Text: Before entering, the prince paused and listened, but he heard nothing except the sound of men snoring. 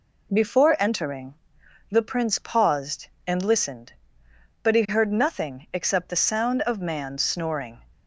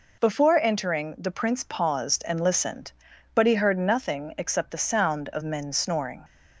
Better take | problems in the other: second | says "man" for "men"; at 6.7 s

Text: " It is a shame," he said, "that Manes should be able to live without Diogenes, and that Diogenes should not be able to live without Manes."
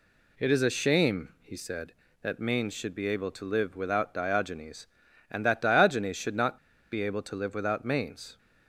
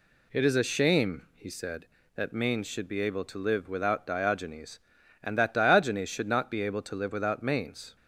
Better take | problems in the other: second | pauses between "not" and "be"; slight; at 6.5 s; 0.32 s long

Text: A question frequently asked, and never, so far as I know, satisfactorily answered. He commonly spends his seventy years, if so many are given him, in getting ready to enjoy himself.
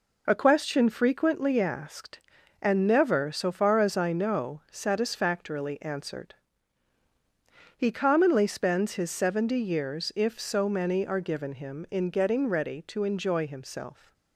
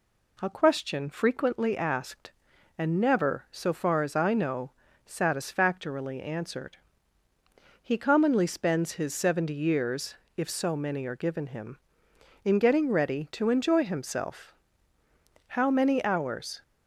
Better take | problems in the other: first | goes on to say "How many hours"; noticeable; from 15.4 s on; 1.1 s long

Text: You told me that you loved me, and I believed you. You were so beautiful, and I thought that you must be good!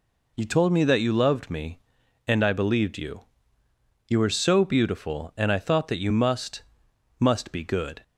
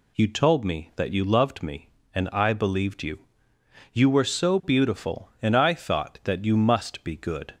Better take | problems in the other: second | says "must" twice; at 7.1 s

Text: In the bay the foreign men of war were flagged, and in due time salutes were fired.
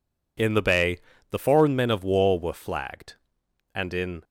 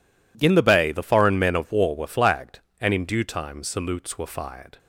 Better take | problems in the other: second | pauses between "bay" and "the"; slight; at 0.9 s; 0.32 s long // stops before "due time salutes were fired"; at 4.2 s

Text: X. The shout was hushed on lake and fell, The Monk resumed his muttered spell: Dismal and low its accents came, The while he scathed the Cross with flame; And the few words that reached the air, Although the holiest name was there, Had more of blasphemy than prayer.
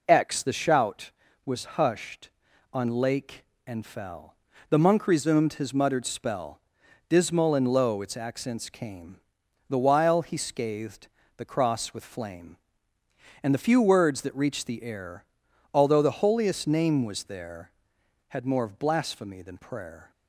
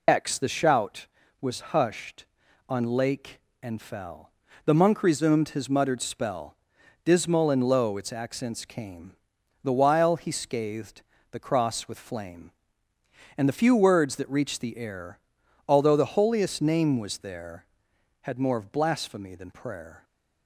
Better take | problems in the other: first | loses the start of "X"; at 0.0 s; 50 ms // pauses between "scathed" and "the"; slight; at 11.0 s; 0.30 s long; slight in the first

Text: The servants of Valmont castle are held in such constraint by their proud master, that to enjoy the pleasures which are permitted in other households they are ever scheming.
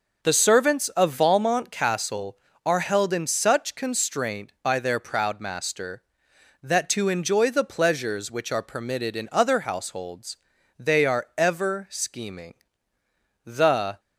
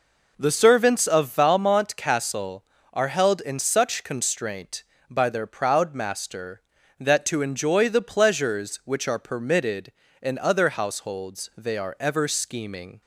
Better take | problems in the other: second | pauses between "households" and "they"; at 10.3 s; 0.42 s long // goes on to say "The"; from 13.4 s on; 0.54 s long

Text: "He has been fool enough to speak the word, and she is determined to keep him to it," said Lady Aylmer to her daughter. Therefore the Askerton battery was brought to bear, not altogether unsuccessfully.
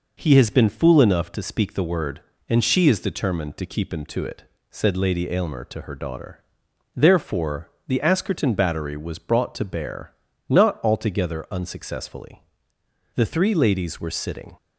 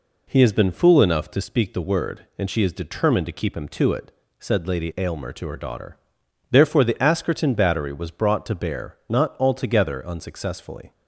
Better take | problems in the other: second | pauses between "Therefore" and "the"; slight; at 7.7 s; 0.16 s long // goes on to say "The three ladies were sitting"; from 13.1 s on; 1.4 s long

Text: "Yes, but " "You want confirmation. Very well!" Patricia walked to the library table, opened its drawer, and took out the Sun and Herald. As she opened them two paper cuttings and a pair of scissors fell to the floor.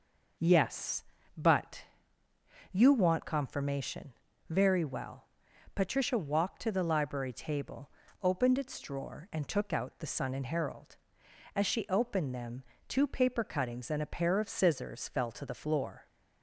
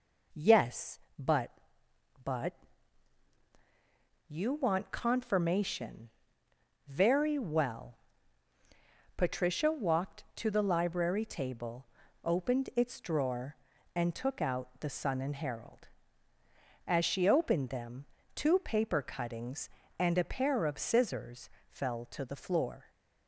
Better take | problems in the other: first | says "but" twice; at 2.2 s // pauses between "them" and "two"; slight; at 18.0 s; 0.28 s long; slight in the first // pauses between "scissors" and "fell"; slight; at 21.4 s; 0.20 s long

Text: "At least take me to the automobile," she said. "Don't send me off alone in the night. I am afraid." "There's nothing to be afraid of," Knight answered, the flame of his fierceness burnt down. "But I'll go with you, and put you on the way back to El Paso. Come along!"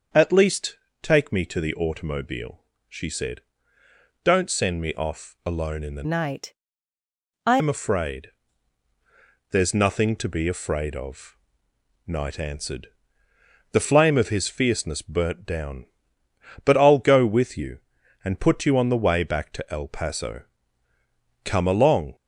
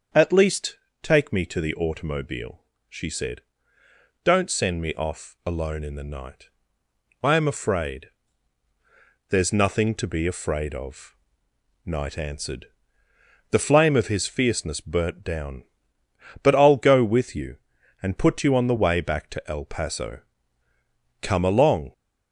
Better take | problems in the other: second | starts louder than the rest; until 1.4 s; 6.5 dB; also in the second // pauses between "least" and "take"; slight; at 0.7 s; 0.26 s long; slight in the second // changes voice from "night" to "I"; from 6.0 to 7.5 s; 1.5 s long

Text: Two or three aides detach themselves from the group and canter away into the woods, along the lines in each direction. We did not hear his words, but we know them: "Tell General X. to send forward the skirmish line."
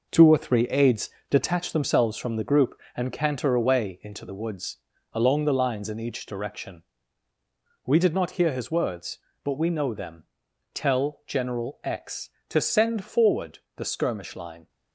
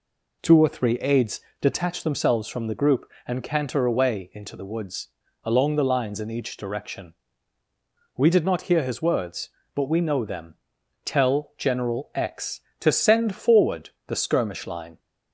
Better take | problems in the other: second | gets quieter; strong; throughout; 7.5 dB // pauses between "aides" and "detach"; slight; at 1.1 s; 0.20 s long; slight in the second // pauses between "forward" and "the"; slight; at 13.5 s; 0.16 s long; slight in the second

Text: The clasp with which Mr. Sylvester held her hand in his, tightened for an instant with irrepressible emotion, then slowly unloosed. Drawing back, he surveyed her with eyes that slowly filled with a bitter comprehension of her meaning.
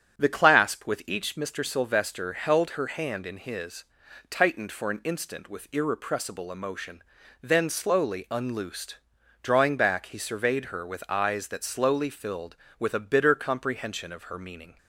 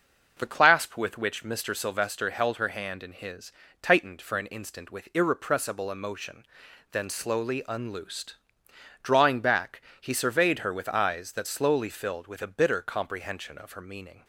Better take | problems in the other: second | starts louder than the rest; strong; until 1.2 s; 7.5 dB // says "each" for "which"; at 1.0 s

